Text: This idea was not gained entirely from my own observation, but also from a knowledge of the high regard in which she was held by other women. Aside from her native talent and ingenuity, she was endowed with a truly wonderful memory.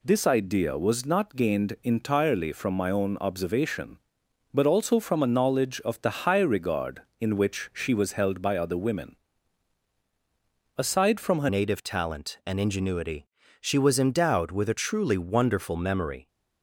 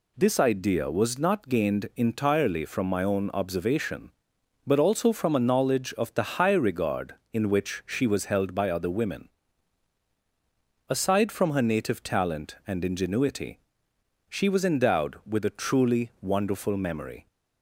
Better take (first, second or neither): second